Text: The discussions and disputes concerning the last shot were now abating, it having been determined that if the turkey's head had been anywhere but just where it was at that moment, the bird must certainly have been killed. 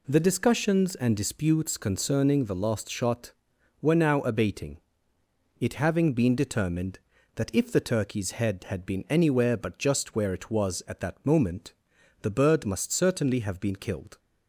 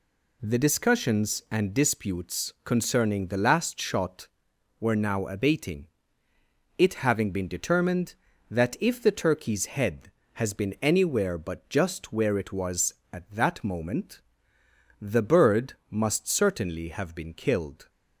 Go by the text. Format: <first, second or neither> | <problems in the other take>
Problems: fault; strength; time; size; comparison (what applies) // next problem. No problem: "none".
first | says "has" for "had"; at 10.3 s // pauses between "bird" and "must"; slight; at 15.7 s; 0.16 s long